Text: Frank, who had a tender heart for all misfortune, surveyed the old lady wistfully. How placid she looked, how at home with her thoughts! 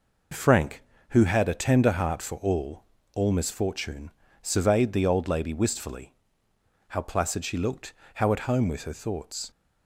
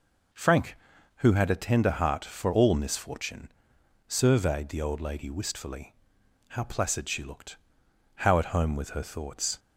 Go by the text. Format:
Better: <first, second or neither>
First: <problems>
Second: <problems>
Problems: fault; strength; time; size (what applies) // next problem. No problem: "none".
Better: second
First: says "all" twice; at 3.1 s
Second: none